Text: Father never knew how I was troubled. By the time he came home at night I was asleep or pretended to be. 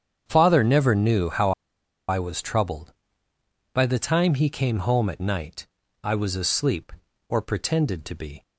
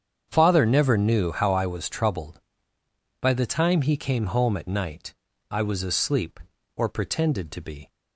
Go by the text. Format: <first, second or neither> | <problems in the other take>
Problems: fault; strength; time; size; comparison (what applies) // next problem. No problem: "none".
second | starts louder than the rest; strong; until 1.2 s; 8 dB; strong in the second // pauses between "how" and "I"; noticeable; at 1.5 s; 0.57 s long // pauses between "night" and "I"; slight; at 5.6 s; 0.34 s long; slight in the second